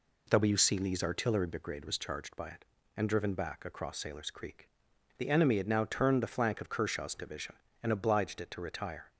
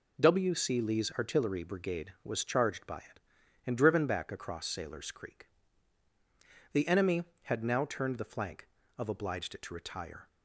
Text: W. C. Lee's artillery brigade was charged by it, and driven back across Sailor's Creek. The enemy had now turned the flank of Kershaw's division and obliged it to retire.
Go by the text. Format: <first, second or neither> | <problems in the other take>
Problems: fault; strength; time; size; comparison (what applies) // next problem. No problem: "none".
first | skips "Kershaw's division and"; at 9.0 s